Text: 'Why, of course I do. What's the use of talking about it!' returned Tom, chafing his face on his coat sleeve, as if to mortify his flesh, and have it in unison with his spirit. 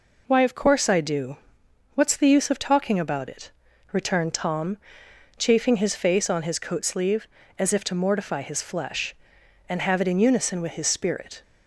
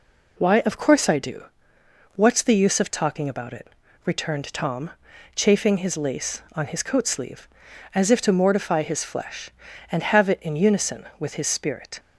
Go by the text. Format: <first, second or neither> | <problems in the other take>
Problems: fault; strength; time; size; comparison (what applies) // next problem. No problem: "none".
first | says "lace" for "face"; at 5.9 s